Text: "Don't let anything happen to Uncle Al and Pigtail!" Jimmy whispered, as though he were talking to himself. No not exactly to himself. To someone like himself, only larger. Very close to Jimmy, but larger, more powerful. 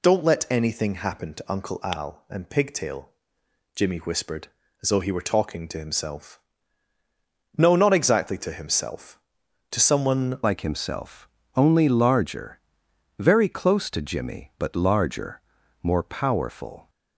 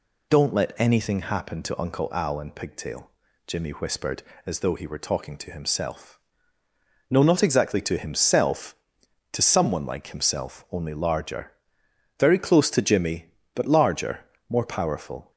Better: second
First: changes voice at "like"; from 10.4 s on; 6.4 s long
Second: none

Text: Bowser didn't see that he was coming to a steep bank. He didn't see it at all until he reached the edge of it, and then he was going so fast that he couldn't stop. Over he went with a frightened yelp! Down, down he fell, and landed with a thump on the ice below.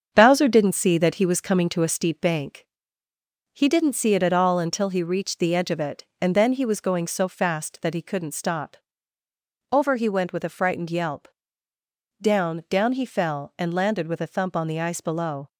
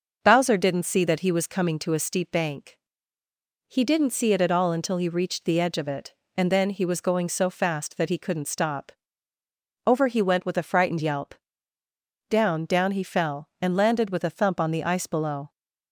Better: second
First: gets quieter; noticeable; throughout; 5.5 dB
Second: none

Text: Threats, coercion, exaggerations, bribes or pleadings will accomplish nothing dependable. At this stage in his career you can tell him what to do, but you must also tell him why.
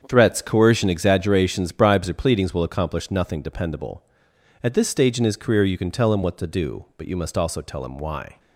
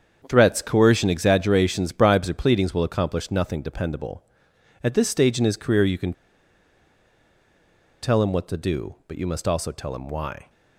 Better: first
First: starts louder than the rest; strong; until 1.0 s; 7.5 dB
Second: starts louder than the rest; strong; until 1.2 s; 7.5 dB // pauses between "can" and "tell"; strong; at 6.1 s; 1.9 s long

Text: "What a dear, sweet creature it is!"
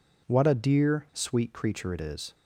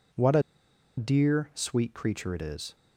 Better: first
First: none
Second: pauses between "a" and "dear"; noticeable; at 0.4 s; 0.55 s long

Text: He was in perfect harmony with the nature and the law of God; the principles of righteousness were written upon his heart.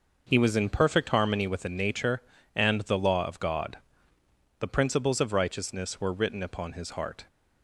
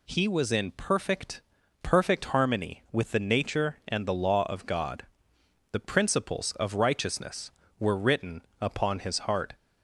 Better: first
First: none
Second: says "perfect" twice; at 1.8 s // pauses between "written" and "upon"; slight; at 8.4 s; 0.18 s long

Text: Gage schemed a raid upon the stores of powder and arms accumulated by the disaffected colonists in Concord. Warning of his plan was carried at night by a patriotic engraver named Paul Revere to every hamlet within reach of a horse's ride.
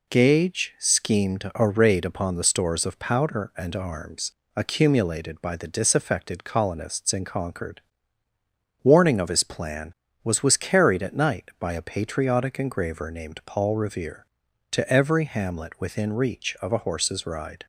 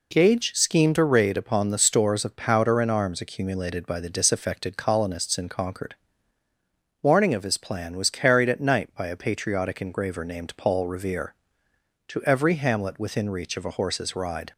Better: second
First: pauses between "arms" and "accumulated"; slight; at 4.3 s; 0.26 s long // says "was" twice; at 10.4 s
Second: none

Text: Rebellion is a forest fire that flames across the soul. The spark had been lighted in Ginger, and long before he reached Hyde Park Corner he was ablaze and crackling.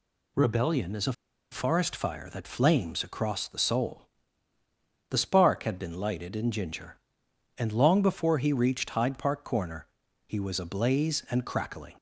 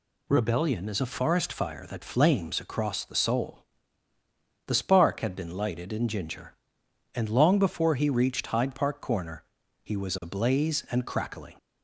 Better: second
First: pauses between "a" and "forest"; at 1.1 s; 0.39 s long // pauses between "Corner" and "he"; at 9.8 s; 0.40 s long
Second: pauses between "Corner" and "he"; at 9.4 s; 0.40 s long

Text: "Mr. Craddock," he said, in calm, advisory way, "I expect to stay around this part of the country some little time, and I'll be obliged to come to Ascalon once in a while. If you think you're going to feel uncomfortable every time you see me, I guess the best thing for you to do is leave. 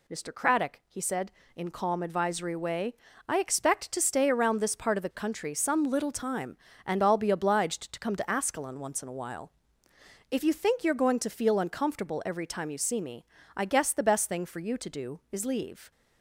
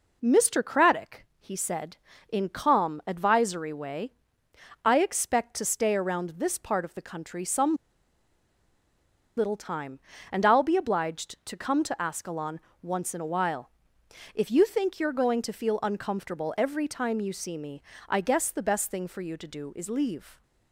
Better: first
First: none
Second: pauses between "some" and "little"; strong; at 7.7 s; 1.6 s long // pauses between "Ascalon" and "once"; slight; at 12.5 s; 0.22 s long

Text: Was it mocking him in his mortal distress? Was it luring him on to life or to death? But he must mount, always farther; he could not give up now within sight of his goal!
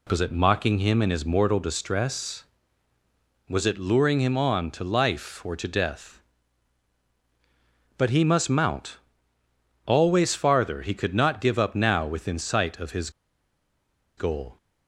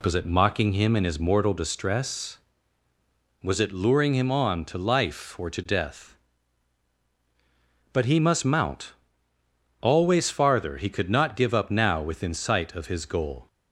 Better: second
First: pauses between "his" and "goal"; at 13.0 s; 1.0 s long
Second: none

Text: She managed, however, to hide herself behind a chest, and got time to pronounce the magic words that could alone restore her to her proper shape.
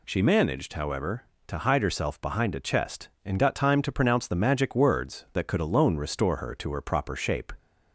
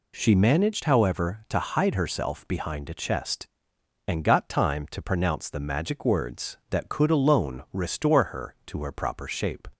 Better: neither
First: none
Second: none

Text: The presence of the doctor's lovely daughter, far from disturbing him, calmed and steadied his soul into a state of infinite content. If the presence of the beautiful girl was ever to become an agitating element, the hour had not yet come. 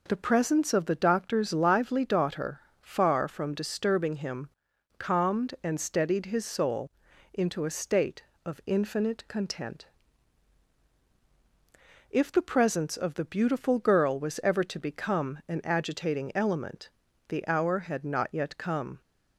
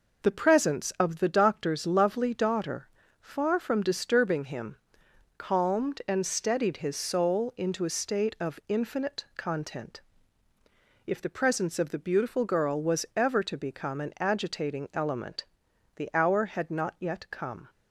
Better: second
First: says "lively" for "lovely"; at 1.5 s // pauses between "soul" and "into"; at 6.8 s; 0.44 s long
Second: none

